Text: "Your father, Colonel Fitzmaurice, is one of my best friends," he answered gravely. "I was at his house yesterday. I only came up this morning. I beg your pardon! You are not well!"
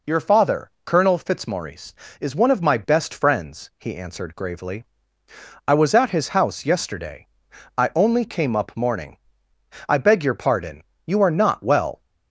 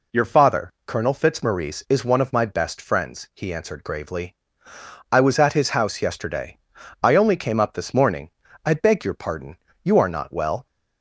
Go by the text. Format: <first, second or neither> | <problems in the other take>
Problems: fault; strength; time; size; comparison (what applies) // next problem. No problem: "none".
second | skips "this"; at 8.7 s